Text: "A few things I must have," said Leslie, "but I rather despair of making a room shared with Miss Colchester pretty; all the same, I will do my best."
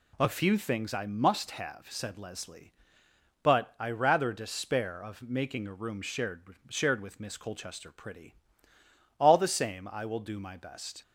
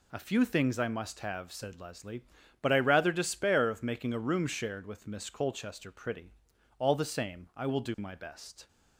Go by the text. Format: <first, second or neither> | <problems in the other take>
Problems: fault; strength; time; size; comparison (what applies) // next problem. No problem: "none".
second | says "shared" twice; at 6.6 s